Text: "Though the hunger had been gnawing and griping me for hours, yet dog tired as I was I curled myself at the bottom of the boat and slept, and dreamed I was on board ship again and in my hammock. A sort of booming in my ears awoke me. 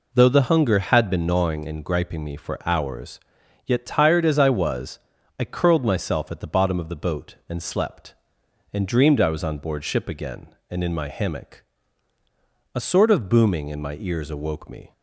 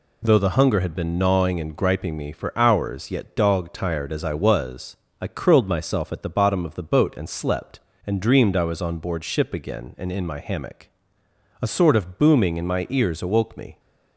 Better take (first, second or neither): second